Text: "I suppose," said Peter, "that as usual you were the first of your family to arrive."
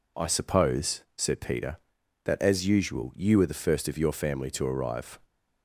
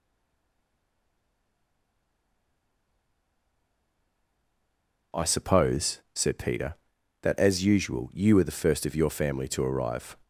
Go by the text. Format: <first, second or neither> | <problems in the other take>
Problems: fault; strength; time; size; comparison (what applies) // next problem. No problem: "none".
first | stays silent before the first word; strong; until 5.1 s; 5.1 s long